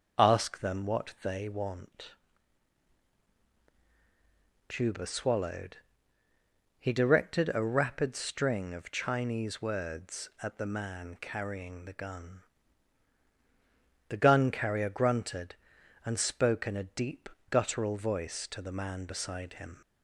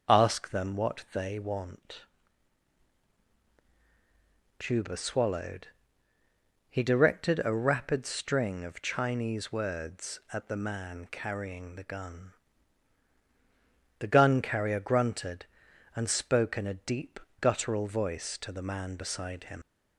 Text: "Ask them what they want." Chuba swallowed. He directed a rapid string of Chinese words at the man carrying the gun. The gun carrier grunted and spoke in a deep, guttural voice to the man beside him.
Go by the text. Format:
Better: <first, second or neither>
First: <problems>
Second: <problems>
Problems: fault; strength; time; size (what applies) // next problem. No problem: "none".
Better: first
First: none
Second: leaves "him" unfinished; at 19.6 s; 95 ms